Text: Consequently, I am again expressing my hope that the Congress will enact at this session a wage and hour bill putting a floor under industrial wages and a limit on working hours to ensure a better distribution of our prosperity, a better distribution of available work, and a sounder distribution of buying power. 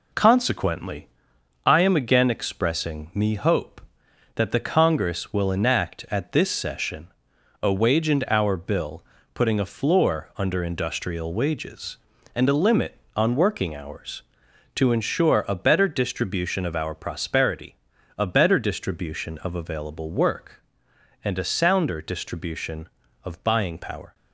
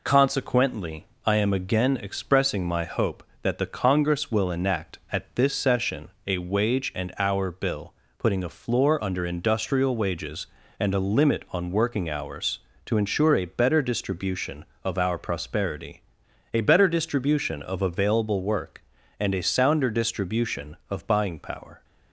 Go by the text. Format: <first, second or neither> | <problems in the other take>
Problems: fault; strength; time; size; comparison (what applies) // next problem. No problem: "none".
second | says "me" for "my"; at 3.1 s // pauses between "session" and "a"; noticeable; at 7.0 s; 0.54 s long; slight in the second // pauses between "bill" and "putting"; slight; at 9.0 s; 0.30 s long; slight in the second